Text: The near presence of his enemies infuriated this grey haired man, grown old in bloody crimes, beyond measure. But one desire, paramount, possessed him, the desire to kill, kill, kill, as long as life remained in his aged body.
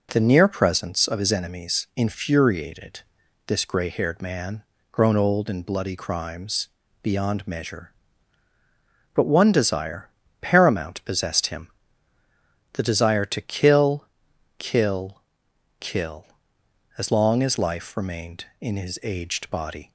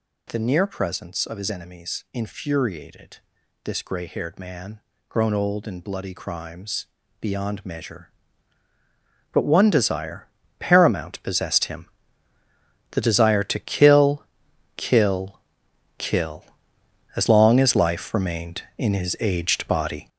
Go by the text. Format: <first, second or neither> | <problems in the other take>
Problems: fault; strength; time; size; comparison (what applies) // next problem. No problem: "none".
first | gets louder; strong; throughout; 8 dB // pauses between "infuriated" and "this"; at 3.1 s; 0.44 s long; also in the first